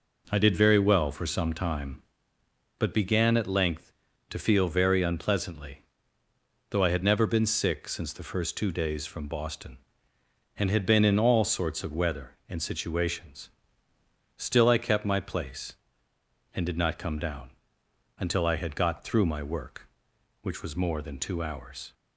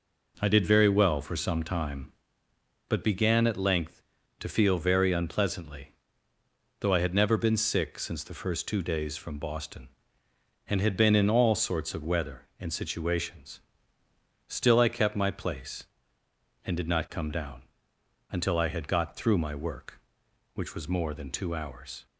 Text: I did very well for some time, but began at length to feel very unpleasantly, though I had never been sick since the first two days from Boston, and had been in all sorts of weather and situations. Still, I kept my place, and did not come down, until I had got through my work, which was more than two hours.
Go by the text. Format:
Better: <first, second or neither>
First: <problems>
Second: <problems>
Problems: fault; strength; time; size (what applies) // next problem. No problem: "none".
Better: neither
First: none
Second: none